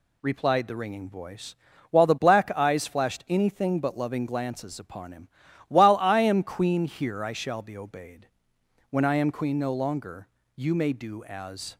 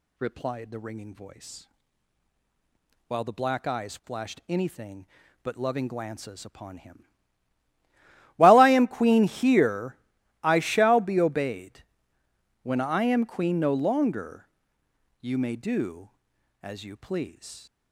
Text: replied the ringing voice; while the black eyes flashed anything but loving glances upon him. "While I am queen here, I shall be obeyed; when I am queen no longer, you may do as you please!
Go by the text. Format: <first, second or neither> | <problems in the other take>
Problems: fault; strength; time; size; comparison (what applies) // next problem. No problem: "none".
second | stops before "you please"; at 11.7 s